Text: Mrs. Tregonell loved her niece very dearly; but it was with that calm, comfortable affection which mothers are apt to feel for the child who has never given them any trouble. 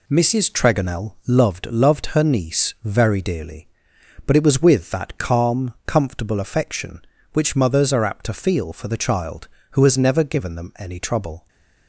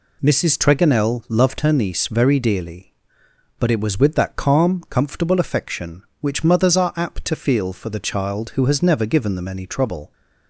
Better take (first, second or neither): second